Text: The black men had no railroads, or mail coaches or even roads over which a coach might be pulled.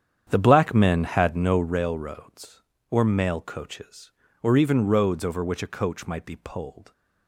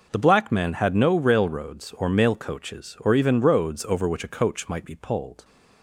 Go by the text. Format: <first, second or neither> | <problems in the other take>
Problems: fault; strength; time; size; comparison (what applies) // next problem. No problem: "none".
second | starts louder than the rest; strong; until 1.8 s; 9 dB